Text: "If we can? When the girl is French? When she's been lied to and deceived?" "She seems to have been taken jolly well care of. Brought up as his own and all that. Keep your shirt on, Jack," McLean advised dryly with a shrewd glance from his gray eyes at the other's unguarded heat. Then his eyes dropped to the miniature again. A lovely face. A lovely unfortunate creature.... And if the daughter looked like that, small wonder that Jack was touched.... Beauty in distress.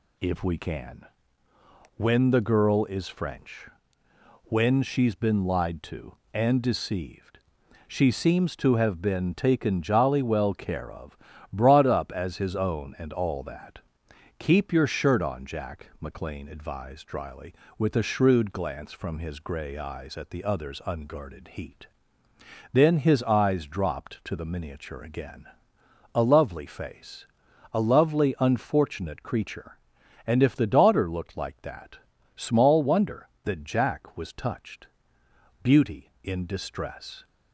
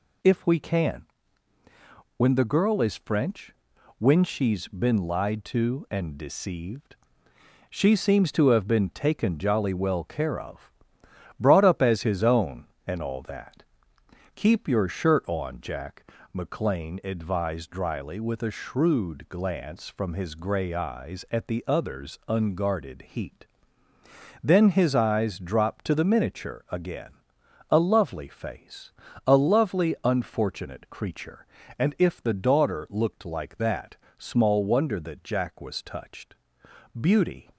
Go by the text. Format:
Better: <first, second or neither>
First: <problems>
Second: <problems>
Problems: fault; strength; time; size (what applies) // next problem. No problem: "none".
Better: first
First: none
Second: stops before "in distress"; at 37.5 s